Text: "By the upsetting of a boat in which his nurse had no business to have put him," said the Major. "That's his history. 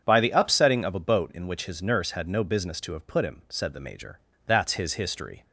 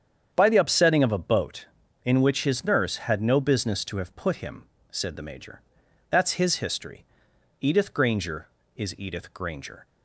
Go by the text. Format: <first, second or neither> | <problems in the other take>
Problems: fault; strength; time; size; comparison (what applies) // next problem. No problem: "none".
first | starts louder than the rest; strong; until 1.3 s; 8 dB; strong in the first // goes on to say "Edith Granger is Edith Granger"; strong; from 7.6 s on; 2.2 s long